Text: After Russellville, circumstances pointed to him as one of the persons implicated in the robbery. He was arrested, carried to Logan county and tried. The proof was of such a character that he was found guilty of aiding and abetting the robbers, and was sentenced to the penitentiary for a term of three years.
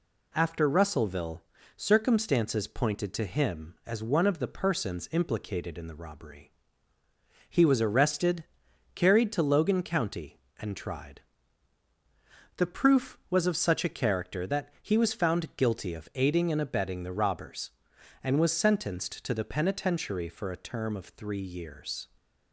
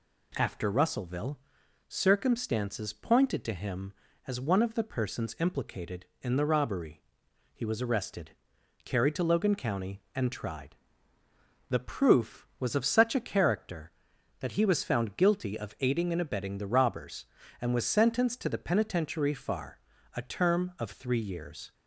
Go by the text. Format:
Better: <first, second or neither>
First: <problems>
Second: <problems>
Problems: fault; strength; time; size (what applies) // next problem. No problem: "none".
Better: first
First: none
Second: says "far" for "for"; at 19.3 s